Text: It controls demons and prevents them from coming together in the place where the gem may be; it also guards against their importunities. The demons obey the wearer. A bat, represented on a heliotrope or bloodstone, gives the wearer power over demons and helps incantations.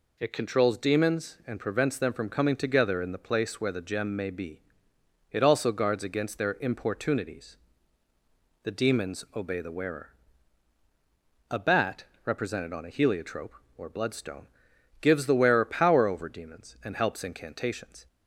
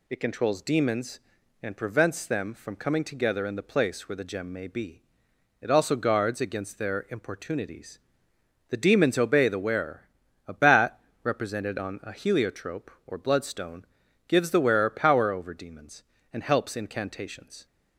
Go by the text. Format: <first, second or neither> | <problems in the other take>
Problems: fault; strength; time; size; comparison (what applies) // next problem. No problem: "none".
neither | none